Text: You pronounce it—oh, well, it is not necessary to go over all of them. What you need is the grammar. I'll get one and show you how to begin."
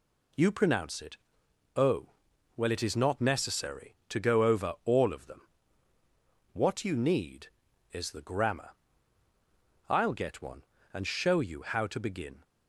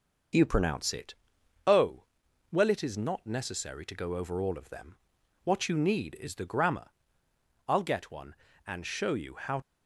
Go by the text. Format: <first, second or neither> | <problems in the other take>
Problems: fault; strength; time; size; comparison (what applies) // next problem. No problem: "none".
first | stops before "to begin"; at 9.6 s